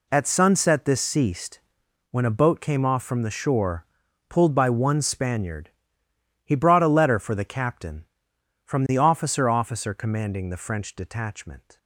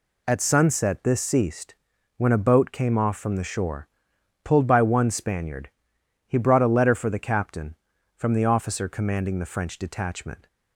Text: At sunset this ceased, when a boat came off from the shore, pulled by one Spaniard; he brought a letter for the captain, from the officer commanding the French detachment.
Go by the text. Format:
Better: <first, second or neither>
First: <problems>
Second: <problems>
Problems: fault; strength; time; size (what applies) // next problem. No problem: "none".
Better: second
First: says "officer" twice; at 9.4 s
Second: none